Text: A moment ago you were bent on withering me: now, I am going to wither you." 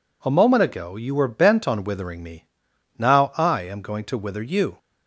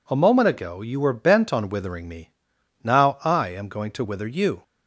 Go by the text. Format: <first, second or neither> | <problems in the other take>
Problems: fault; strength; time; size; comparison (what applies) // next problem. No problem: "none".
neither | none